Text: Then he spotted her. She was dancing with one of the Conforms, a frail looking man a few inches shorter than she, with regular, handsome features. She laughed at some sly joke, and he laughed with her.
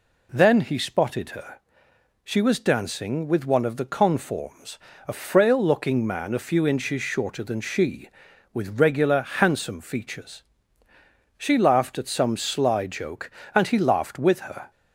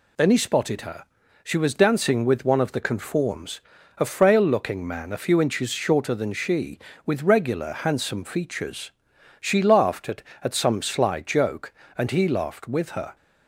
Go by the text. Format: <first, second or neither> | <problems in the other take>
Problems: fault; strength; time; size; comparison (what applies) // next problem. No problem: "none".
first | says "at" twice; at 10.4 s